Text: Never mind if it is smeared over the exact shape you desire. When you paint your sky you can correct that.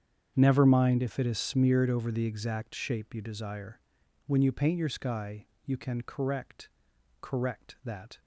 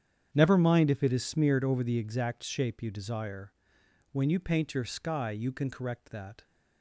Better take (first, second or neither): second